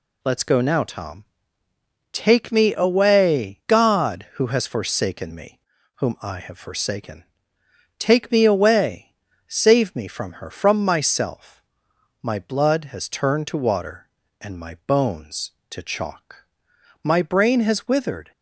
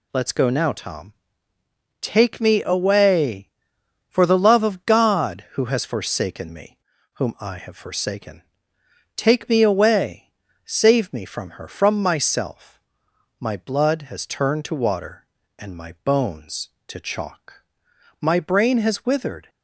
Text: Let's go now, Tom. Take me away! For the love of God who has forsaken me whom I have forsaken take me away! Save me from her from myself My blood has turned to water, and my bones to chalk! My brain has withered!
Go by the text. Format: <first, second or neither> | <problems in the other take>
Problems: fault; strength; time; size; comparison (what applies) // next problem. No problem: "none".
second | skips "For the love of"; at 3.6 s // pauses between "me" and "whom"; slight; at 5.5 s; 0.36 s long; slight in the second // pauses between "forsaken" and "take"; noticeable; at 7.2 s; 0.74 s long; noticeable in the second // pauses between "myself" and "My"; noticeable; at 11.6 s; 0.60 s long; noticeable in the second